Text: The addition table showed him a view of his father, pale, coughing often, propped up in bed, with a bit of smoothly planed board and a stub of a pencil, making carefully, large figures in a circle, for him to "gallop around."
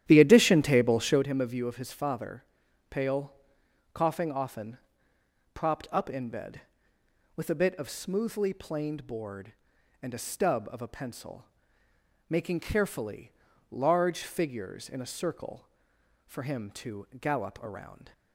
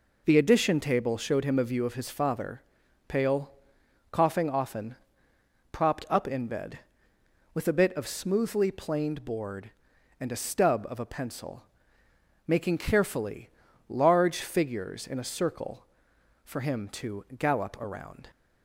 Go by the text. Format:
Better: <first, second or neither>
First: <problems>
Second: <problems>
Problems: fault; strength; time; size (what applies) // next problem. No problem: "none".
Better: second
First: starts louder than the rest; strong; until 1.2 s; 11.5 dB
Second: none